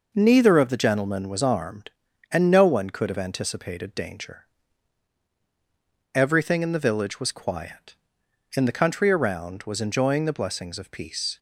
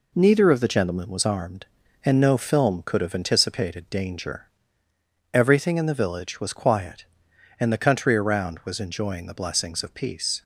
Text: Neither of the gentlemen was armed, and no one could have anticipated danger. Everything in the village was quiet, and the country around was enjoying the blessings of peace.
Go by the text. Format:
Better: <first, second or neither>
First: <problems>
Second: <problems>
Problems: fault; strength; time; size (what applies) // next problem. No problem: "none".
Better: first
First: none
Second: says "film" for "one"; at 2.3 s